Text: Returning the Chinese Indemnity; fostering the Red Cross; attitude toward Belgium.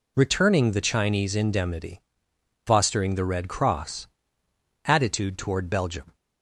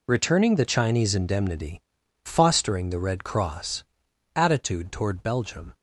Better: neither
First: none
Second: none

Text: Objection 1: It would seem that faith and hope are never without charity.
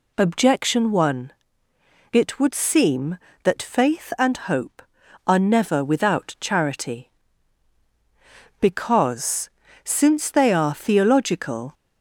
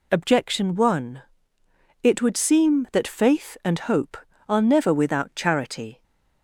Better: second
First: goes on to say "Because since they are theological"; strong; from 8.5 s on; 3.1 s long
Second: none

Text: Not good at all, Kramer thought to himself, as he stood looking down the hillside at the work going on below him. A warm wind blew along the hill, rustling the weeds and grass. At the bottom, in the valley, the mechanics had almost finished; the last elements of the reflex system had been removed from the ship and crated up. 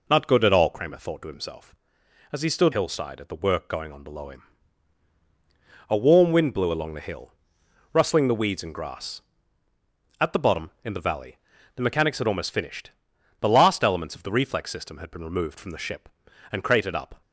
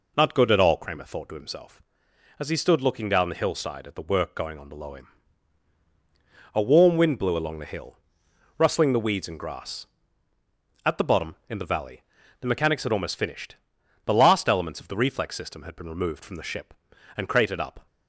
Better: second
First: skips "looking down the"; at 2.7 s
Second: none

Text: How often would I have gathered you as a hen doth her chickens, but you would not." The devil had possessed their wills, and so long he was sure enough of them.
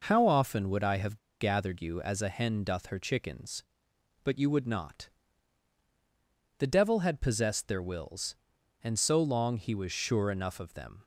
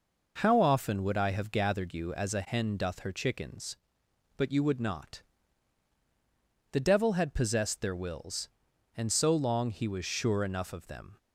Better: second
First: pauses between "have" and "gathered"; slight; at 1.1 s; 0.23 s long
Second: none

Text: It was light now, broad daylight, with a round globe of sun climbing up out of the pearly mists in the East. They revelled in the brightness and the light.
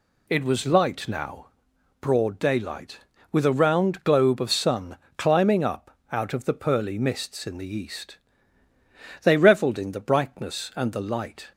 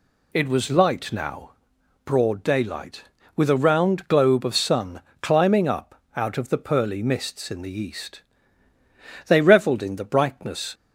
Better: first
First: pauses between "sun" and "climbing"; slight; at 4.9 s; 0.20 s long // pauses between "up" and "out"; slight; at 5.9 s; 0.16 s long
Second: pauses between "sun" and "climbing"; slight; at 5.0 s; 0.20 s long // pauses between "up" and "out"; slight; at 5.9 s; 0.16 s long // stops before "and the light"; at 10.7 s

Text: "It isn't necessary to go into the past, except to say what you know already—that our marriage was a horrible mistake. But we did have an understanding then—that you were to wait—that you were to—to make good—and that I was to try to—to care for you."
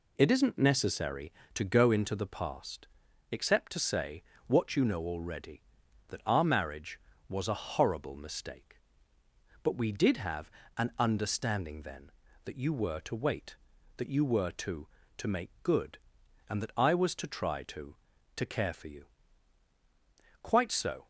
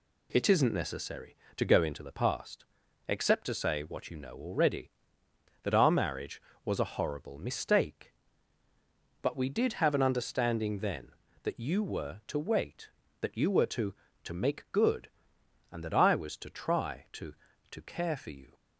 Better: second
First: pauses between "say" and "what"; slight; at 4.2 s; 0.24 s long // pauses between "have" and "an"; slight; at 10.4 s; 0.28 s long // goes on to say "Quite so"; noticeable; from 20.4 s on; 0.66 s long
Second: none

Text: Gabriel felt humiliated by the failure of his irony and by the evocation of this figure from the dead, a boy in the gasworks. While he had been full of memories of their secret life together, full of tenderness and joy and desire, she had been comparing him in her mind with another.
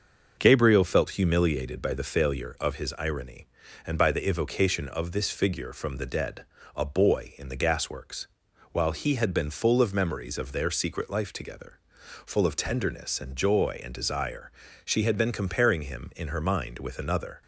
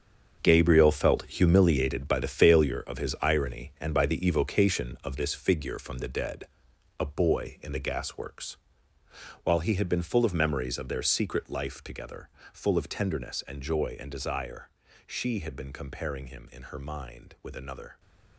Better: first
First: starts louder than the rest; noticeable; until 1.4 s; 6 dB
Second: gets quieter; strong; throughout; 11.5 dB // starts louder than the rest; strong; until 1.4 s; 7.5 dB

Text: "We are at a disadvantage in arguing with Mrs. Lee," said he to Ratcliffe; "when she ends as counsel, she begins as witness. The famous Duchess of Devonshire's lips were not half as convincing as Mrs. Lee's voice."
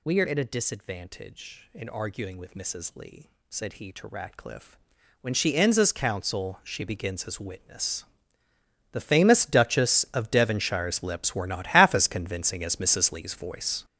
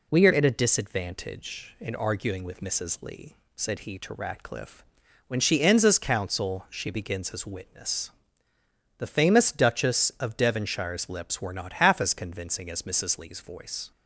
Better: second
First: gets louder; strong; throughout; 10.5 dB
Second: none

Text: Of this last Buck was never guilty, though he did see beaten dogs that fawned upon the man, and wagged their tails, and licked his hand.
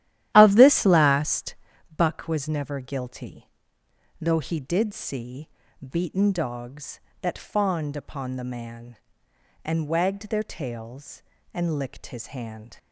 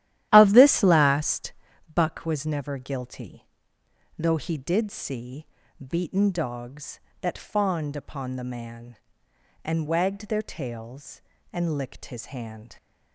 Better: neither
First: starts louder than the rest; strong; until 1.3 s; 13 dB // pauses between "last" and "Buck"; at 1.5 s; 0.38 s long // pauses between "see" and "beaten"; slight; at 5.4 s; 0.35 s long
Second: starts louder than the rest; strong; until 1.3 s; 13 dB // pauses between "last" and "Buck"; at 1.5 s; 0.38 s long // pauses between "see" and "beaten"; slight; at 5.4 s; 0.36 s long

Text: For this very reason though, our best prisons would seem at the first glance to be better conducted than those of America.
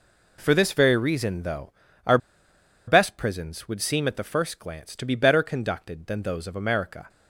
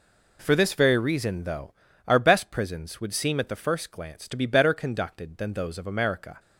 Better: second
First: pauses between "our" and "best"; noticeable; at 2.1 s; 0.70 s long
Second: none

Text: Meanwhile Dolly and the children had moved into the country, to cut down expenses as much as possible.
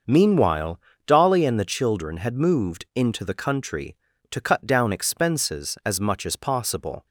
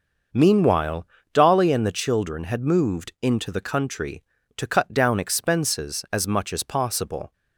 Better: neither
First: starts louder than the rest; noticeable; until 1.3 s; 6 dB // pauses between "Meanwhile" and "Dolly"; slight; at 0.8 s; 0.26 s long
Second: starts louder than the rest; noticeable; until 1.5 s; 6 dB // pauses between "Meanwhile" and "Dolly"; slight; at 1.0 s; 0.26 s long

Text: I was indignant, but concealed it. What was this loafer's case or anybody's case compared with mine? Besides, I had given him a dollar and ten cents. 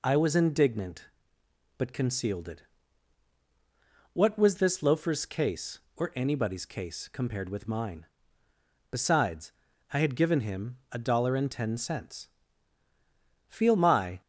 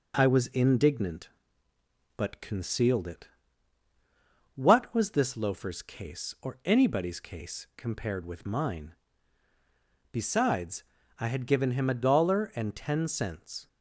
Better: second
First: goes on to say "Feel my"; noticeable; from 13.4 s on; 0.72 s long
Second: none

